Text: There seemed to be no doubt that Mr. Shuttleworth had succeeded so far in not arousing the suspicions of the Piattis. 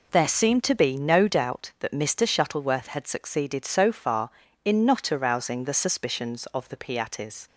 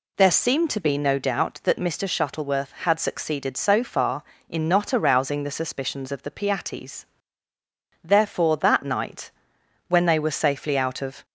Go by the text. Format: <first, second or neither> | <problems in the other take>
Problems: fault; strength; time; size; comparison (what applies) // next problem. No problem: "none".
first | goes on to say "Therefore that night when they were safely out of"; strong; from 8.0 s on; 3.2 s long